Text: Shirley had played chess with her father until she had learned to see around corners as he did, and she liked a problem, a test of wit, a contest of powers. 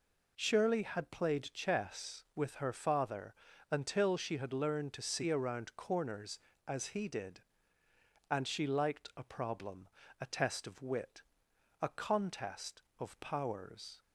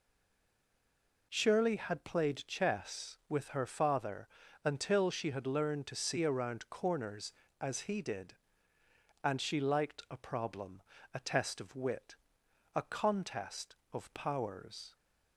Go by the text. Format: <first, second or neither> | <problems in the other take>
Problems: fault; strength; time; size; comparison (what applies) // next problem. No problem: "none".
first | stays silent before the first word; noticeable; until 1.3 s; 1.3 s long // pauses between "father" and "until"; at 4.2 s; 0.38 s long; also in the first